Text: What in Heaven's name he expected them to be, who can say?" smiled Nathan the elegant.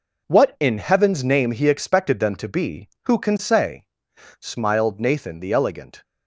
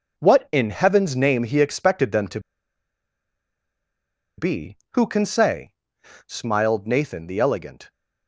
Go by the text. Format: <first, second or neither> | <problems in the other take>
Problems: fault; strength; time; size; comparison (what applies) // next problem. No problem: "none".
first | pauses between "to" and "be"; strong; at 2.4 s; 1.9 s long